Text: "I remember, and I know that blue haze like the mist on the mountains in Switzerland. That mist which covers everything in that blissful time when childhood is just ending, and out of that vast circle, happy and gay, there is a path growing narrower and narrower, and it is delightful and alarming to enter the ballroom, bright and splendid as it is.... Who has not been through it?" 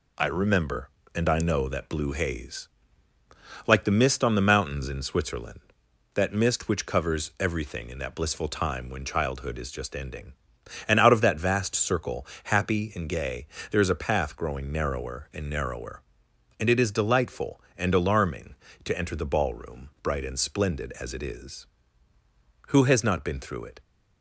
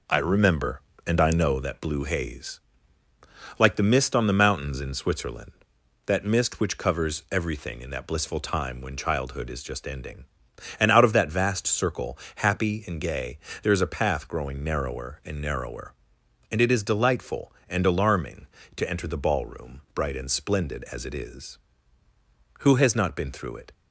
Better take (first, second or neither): first